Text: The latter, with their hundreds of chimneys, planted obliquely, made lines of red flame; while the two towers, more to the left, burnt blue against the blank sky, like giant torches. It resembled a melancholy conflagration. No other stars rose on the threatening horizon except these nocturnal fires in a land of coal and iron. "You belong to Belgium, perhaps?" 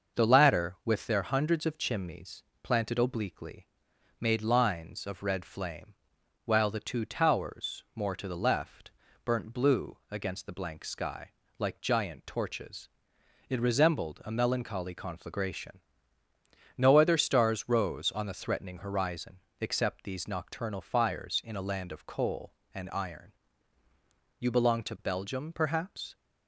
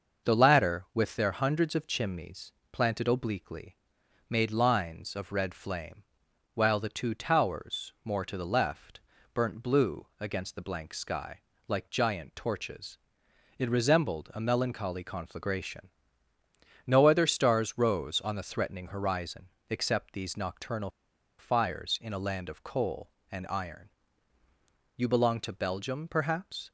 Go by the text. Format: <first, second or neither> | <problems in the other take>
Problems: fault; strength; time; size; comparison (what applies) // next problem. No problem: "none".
first | starts louder than the rest; noticeable; until 1.3 s; 6 dB; noticeable in the first // pauses between "horizon" and "except"; slight; at 19.4 s; 0.20 s long; slight in the first // pauses between "nocturnal" and "fires"; noticeable; at 20.8 s; 0.49 s long